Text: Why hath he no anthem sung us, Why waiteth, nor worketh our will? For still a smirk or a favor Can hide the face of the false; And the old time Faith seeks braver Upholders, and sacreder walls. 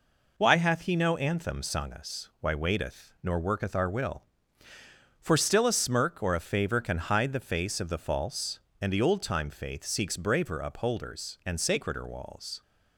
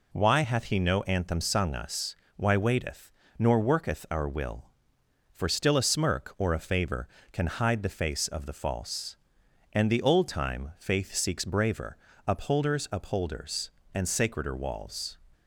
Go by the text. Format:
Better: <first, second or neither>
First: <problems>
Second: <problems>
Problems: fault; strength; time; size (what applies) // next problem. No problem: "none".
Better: first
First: none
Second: pauses between "braver" and "Upholders"; slight; at 11.9 s; 0.30 s long // says "Upholders" twice; at 12.9 s